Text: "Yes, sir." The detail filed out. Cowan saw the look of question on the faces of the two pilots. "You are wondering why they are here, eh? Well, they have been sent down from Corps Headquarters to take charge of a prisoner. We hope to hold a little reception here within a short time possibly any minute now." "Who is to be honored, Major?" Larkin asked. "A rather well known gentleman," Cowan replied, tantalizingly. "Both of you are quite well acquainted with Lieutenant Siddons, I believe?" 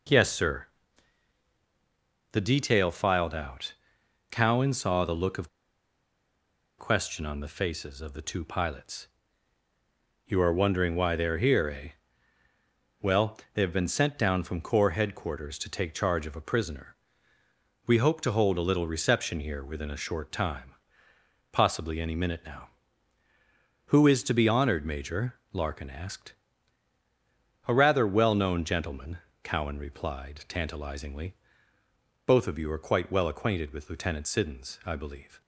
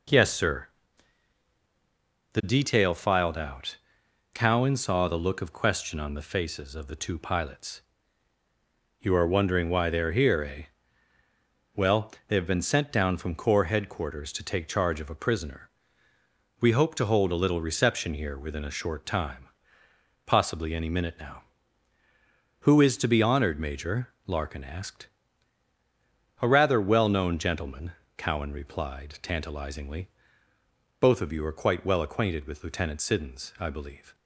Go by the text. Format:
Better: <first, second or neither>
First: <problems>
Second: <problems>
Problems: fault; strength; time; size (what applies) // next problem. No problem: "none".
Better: second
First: pauses between "of" and "question"; strong; at 5.4 s; 1.2 s long // pauses between "time" and "possibly"; noticeable; at 20.7 s; 0.78 s long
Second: pauses between "time" and "possibly"; noticeable; at 19.4 s; 0.78 s long